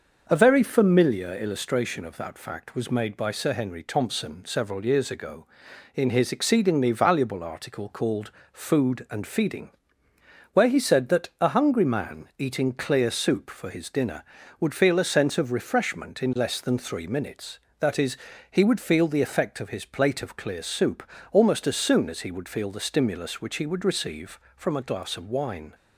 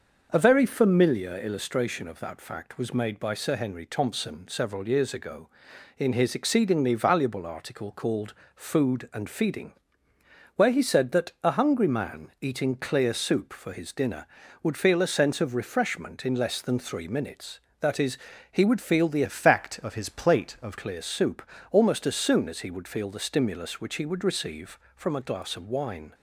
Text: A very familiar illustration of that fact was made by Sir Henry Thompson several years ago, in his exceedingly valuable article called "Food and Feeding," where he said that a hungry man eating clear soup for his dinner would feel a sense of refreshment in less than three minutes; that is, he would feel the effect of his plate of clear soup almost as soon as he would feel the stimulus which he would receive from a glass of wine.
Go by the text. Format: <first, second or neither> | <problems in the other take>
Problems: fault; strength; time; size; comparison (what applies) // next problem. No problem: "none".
first | starts louder than the rest; until 1.3 s; 6 dB; also in the first // pauses between "called" and "Food"; slight; at 8.3 s; 0.20 s long; slight in the first // changes voice from "effect" to "of"; from 19.2 to 20.7 s; 1.5 s long // pauses between "soup" and "almost"; slight; at 21.4 s; 0.30 s long; slight in the first